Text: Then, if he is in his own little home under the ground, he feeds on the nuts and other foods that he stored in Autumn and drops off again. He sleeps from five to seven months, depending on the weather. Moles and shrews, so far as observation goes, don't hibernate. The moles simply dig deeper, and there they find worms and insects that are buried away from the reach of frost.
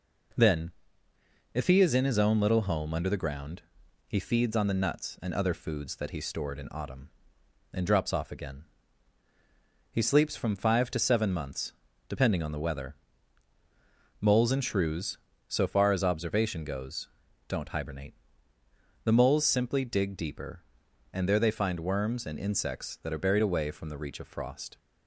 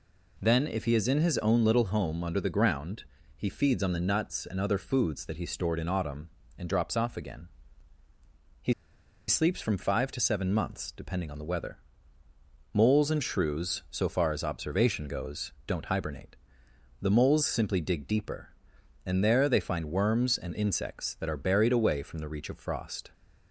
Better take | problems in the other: first | pauses between "He" and "sleeps"; noticeable; at 8.7 s; 0.55 s long

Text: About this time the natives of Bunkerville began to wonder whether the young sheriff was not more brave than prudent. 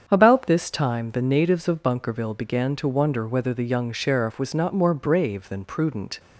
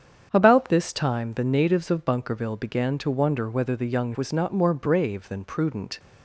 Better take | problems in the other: first | starts louder than the rest; strong; until 1.3 s; 8 dB; strong in the first // skips "sheriff"; at 4.1 s

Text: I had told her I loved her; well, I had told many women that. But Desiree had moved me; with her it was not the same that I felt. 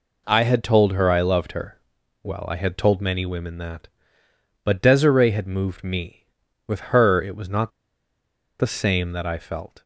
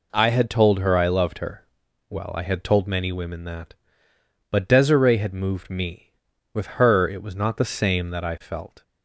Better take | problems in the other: second | pauses between "not" and "the"; noticeable; at 7.7 s; 0.89 s long

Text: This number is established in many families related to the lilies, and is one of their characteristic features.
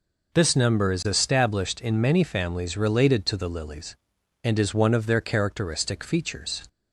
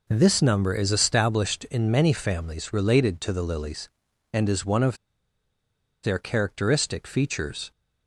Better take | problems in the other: first | pauses between "of" and "their"; at 4.9 s; 1.0 s long

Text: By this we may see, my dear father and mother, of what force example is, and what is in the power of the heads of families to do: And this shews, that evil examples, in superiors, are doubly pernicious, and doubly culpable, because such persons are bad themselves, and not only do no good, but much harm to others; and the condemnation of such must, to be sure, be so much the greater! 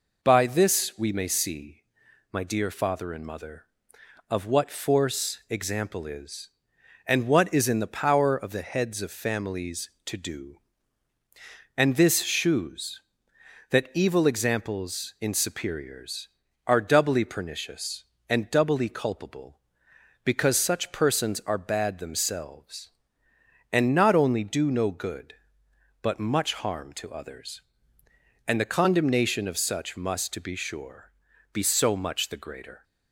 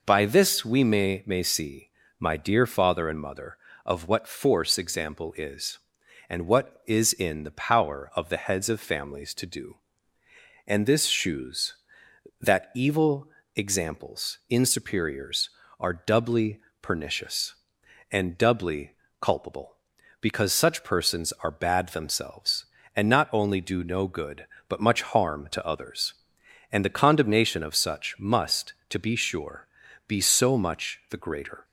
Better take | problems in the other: first | says "may" twice; at 1.2 s // pauses between "evil" and "examples"; slight; at 13.2 s; 0.26 s long // pauses between "doubly" and "pernicious"; slight; at 16.6 s; 0.22 s long // pauses between "doubly" and "culpable"; slight; at 18.9 s; 0.30 s long

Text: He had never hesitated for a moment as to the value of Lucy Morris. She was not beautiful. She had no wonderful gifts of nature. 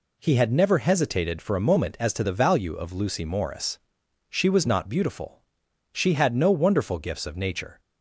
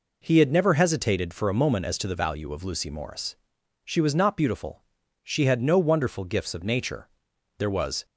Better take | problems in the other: first | goes on to say "There was"; slight; from 7.5 s on; 0.48 s long

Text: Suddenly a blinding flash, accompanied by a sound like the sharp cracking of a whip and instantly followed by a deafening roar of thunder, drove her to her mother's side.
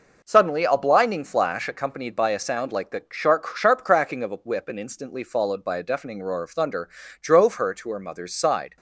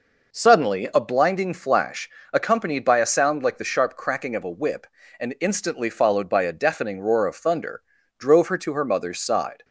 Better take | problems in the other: second | says "sharp" twice; at 3.5 s

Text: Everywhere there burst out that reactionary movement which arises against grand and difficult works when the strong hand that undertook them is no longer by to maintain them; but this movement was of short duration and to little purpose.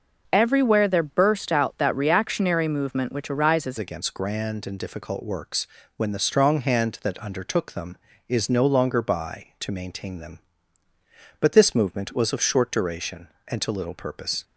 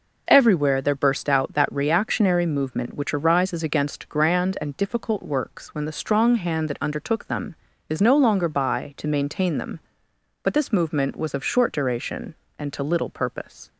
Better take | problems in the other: second | changes voice at "against"; from 3.7 s on; 10.7 s long // pauses between "works" and "when"; slight; at 5.6 s; 0.30 s long

